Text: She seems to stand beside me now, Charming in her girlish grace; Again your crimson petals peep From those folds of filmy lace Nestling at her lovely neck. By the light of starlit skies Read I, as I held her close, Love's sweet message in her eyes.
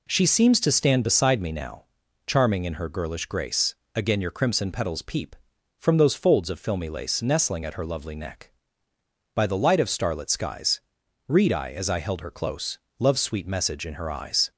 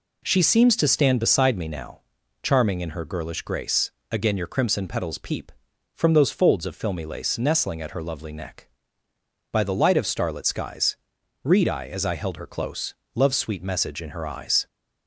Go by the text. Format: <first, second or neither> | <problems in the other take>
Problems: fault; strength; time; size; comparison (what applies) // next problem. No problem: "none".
neither | pauses between "skies" and "Read"; noticeable; the same in both